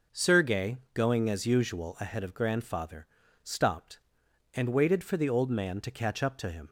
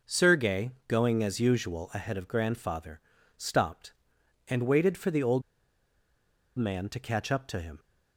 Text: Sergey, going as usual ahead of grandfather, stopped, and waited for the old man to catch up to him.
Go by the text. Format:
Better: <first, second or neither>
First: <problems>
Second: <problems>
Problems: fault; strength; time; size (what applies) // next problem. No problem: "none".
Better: first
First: none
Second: pauses between "old" and "man"; at 5.4 s; 1.1 s long